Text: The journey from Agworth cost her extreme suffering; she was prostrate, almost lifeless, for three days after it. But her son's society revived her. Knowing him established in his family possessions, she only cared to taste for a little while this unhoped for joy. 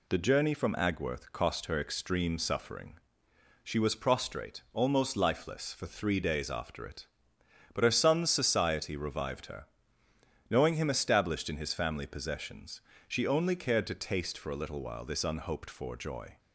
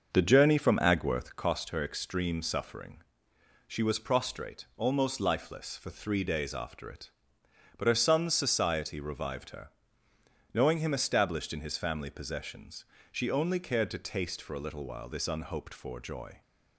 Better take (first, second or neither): first